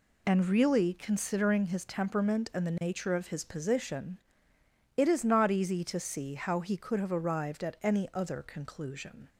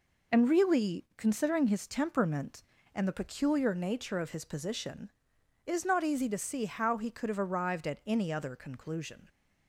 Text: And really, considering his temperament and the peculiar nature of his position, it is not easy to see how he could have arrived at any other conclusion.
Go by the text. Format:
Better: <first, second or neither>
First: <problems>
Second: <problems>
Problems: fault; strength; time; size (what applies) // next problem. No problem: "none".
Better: second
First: skips "peculiar"; at 2.7 s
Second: none